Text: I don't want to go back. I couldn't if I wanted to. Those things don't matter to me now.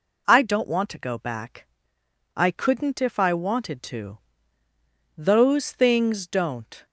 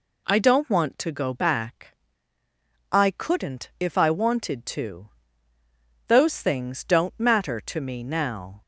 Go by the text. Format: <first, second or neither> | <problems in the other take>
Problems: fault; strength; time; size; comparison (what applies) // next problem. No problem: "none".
second | stops before "matter to me now"; at 6.8 s